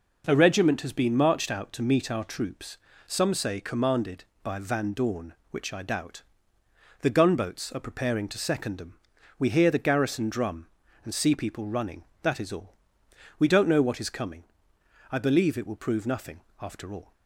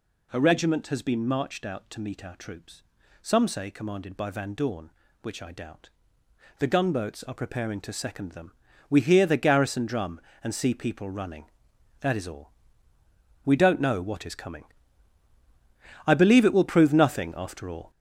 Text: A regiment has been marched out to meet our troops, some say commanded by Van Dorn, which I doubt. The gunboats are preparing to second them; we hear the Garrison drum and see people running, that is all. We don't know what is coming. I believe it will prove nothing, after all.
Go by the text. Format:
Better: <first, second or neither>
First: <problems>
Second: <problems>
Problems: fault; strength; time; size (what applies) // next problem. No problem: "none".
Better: first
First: none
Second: gets louder; strong; throughout; 7.5 dB